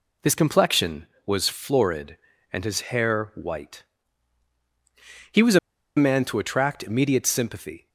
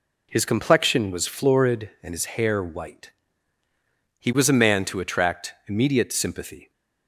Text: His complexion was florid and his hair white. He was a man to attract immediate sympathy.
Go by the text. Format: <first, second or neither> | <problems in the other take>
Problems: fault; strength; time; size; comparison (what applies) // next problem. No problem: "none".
second | pauses between "a" and "man"; at 5.5 s; 0.39 s long